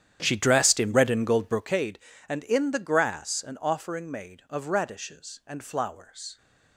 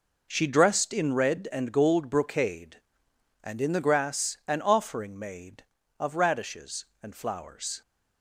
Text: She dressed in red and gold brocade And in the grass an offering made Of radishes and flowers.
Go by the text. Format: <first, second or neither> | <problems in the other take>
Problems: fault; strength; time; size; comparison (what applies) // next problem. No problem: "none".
second | starts louder than the rest; strong; until 1.9 s; 10 dB